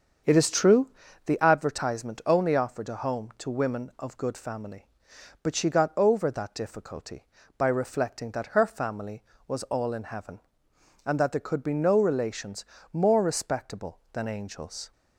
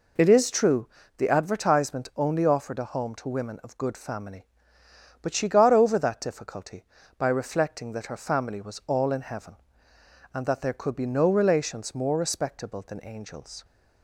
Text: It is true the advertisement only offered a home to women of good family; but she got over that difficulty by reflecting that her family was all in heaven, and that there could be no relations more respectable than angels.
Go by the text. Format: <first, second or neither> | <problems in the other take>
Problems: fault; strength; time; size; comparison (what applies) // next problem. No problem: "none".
second | starts louder than the rest; until 1.4 s; 7 dB // pauses between "true" and "the"; at 0.8 s; 0.38 s long; slight in the second // pauses between "relations" and "more"; slight; at 12.6 s; 0.30 s long